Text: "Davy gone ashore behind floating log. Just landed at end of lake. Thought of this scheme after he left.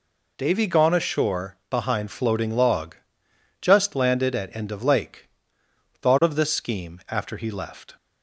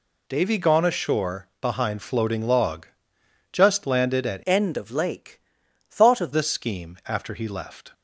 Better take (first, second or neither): first